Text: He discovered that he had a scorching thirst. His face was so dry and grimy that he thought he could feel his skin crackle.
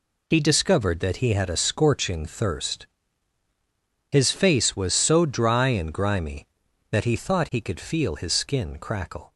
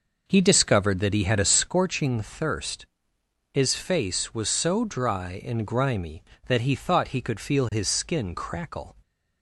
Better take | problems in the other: first | starts louder than the rest; noticeable; until 1.8 s; 5.5 dB

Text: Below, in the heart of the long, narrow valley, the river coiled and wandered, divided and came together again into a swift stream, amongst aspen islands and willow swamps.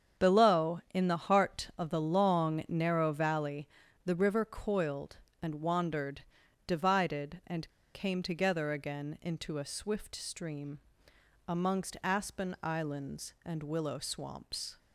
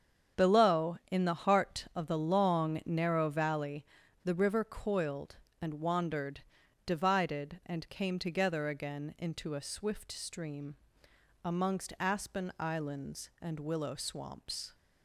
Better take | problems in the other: second | starts louder than the rest; strong; until 1.3 s; 7.5 dB; strong in the second // pauses between "and" and "came"; slight; at 7.6 s; 0.23 s long

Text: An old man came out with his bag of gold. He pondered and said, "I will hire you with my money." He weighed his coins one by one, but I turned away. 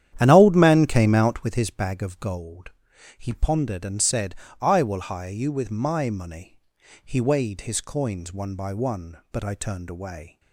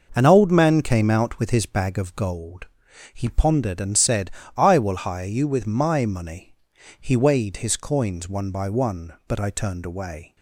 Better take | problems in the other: second | starts louder than the rest; strong; until 1.5 s; 10.5 dB

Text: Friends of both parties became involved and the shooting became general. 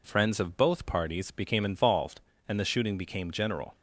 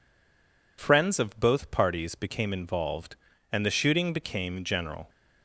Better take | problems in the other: first | stays silent before the first word; slight; until 0.7 s; 0.7 s long

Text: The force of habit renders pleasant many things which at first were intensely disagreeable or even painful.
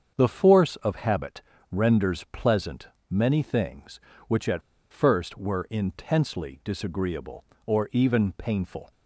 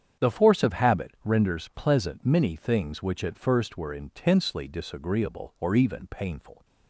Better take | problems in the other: second | starts louder than the rest; strong; until 1.1 s; 7 dB; strong in the second // pauses between "habit" and "renders"; slight; at 1.4 s; 0.30 s long // pauses between "pleasant" and "many"; slight; at 2.8 s; 0.22 s long // pauses between "at" and "first"; slight; at 4.6 s; 0.29 s long

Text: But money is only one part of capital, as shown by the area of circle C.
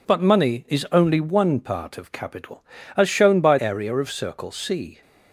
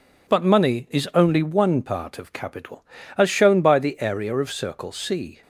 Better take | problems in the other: second | skips "the"; at 3.5 s

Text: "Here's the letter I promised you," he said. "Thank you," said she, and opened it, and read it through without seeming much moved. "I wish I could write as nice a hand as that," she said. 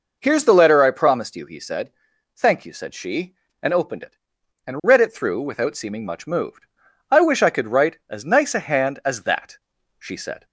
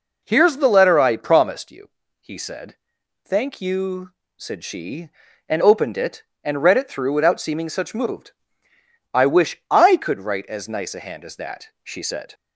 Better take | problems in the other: first | says "such" for "much"; at 7.6 s

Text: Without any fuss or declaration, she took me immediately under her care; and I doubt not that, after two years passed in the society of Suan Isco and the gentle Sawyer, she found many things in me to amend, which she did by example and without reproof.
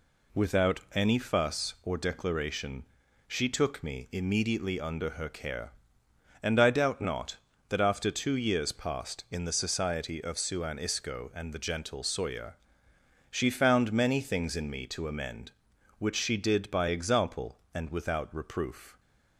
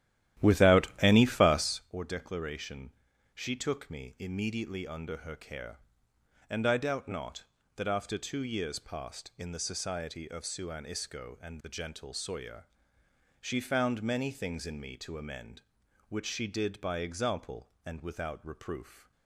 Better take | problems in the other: first | starts louder than the rest; strong; until 1.8 s; 12.5 dB // pauses between "Without" and "any"; slight; at 0.8 s; 0.16 s long; slight in the first

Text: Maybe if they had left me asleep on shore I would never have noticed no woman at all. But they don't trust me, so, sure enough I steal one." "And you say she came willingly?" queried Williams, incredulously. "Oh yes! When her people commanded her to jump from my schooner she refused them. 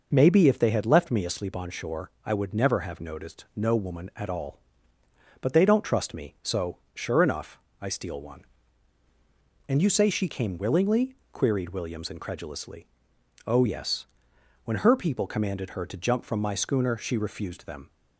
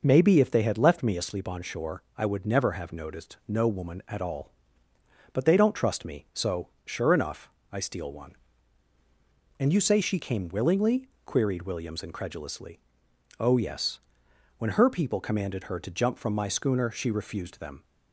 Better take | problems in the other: neither | pauses between "shore" and "I"; slight; the same in both // pauses between "enough" and "I"; slight; the same in both

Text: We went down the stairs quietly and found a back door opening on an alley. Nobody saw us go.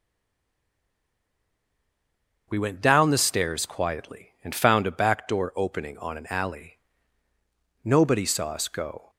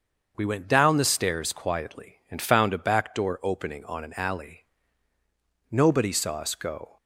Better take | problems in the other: second | stays silent before the first word; until 2.4 s; 2.4 s long // starts louder than the rest; until 3.5 s; 6.5 dB; also in the second

